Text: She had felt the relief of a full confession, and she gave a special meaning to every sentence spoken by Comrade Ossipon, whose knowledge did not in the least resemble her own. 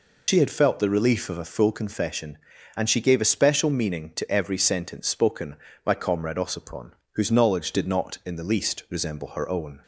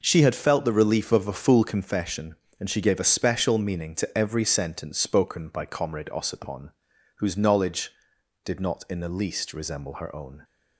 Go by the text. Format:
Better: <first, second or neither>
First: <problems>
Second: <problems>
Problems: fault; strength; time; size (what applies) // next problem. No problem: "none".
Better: second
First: loses the start of "She"; at 0.2 s; 40 ms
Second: none